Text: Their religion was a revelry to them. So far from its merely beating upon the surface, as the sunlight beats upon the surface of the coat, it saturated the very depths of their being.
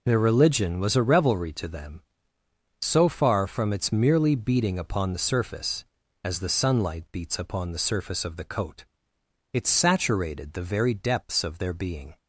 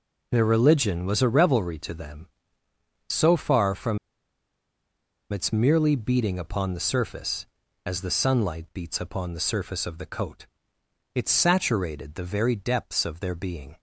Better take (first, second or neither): first